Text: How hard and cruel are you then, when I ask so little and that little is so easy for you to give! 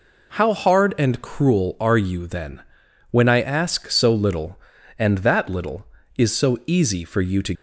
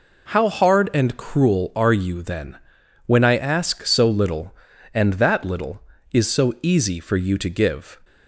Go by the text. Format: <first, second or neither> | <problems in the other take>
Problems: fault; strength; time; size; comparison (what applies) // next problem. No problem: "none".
second | stops before "give"; at 7.5 s